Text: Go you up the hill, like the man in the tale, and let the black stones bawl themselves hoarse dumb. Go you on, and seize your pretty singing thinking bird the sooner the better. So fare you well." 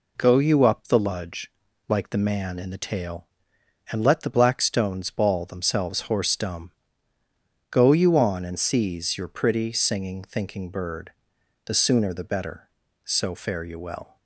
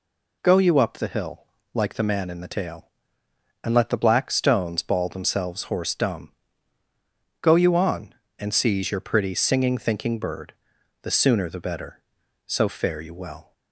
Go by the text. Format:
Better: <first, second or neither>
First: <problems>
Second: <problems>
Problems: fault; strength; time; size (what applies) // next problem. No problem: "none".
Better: second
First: says "ludge" for "hill"; at 0.9 s // pauses between "bird" and "the"; noticeable; at 11.1 s; 0.54 s long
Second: pauses between "bird" and "the"; noticeable; at 10.5 s; 0.48 s long